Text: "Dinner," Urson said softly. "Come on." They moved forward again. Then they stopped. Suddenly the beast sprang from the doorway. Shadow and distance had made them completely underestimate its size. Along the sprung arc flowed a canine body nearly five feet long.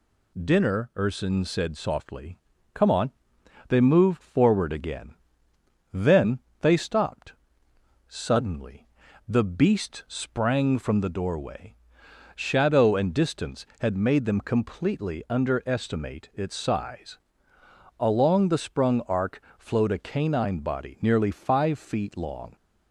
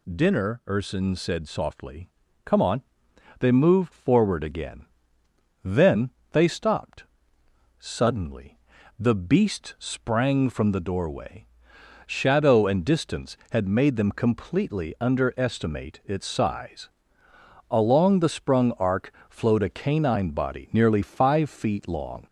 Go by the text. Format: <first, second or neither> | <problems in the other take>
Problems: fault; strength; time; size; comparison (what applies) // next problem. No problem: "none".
first | gets louder; slight; throughout; 2 dB // pauses between "Then" and "they"; slight; at 6.0 s; 0.22 s long; slight in the first // pauses between "Suddenly" and "the"; at 8.5 s; 0.40 s long; also in the first // pauses between "arc" and "flowed"; slight; at 19.1 s; 0.18 s long; slight in the first